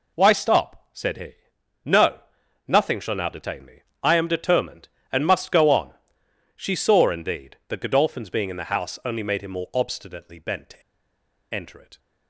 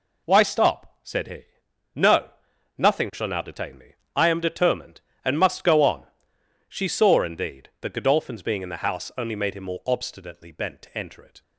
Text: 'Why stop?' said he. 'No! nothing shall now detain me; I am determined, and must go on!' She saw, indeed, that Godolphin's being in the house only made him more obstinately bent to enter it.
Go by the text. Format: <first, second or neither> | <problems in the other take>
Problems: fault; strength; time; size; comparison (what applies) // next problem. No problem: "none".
second | pauses between "to" and "enter"; noticeable; at 10.8 s; 0.72 s long